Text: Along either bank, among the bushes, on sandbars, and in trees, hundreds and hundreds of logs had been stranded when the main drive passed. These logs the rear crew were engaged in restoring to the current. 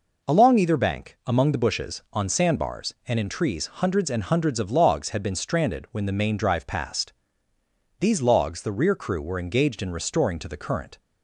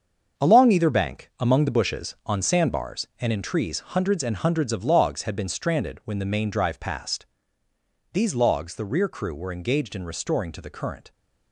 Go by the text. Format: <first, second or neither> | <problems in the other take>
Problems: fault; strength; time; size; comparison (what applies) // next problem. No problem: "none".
first | gets quieter; strong; throughout; 8.5 dB